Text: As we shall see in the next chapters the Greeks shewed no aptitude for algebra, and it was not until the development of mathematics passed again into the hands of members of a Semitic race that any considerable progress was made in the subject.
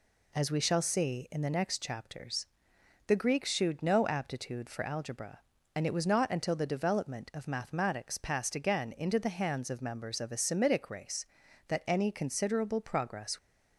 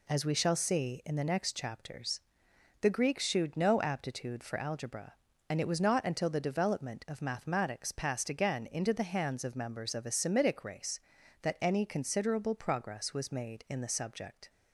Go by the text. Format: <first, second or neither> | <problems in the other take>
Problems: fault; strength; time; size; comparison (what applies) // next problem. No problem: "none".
second | pauses between "chapters" and "the"; noticeable; at 2.4 s; 0.58 s long; noticeable in the second // stops before "was made in the subject"; at 13.3 s